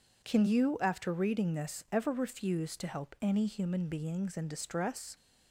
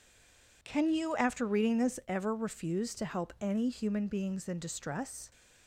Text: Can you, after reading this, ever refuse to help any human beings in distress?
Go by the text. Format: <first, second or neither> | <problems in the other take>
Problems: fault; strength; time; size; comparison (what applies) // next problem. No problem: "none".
first | stays silent before the first word; slight; until 0.6 s; 0.6 s long